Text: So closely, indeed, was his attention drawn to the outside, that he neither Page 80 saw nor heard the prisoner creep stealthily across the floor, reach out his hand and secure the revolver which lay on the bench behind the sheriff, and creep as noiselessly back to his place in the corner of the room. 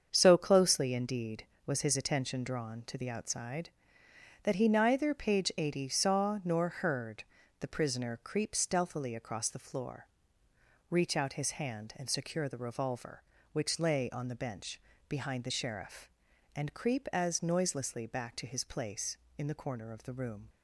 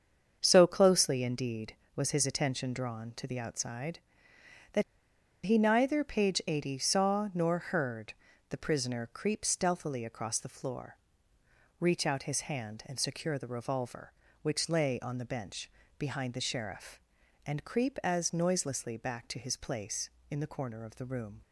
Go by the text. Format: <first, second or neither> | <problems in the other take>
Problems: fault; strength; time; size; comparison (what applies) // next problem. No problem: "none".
first | starts louder than the rest; strong; until 1.4 s; 7 dB; strong in the first // pauses between "that" and "he"; noticeable; at 4.8 s; 0.63 s long // pauses between "heard" and "the"; at 8.1 s; 0.38 s long; also in the first // pauses between "bench" and "behind"; slight; at 15.7 s; 0.26 s long; slight in the first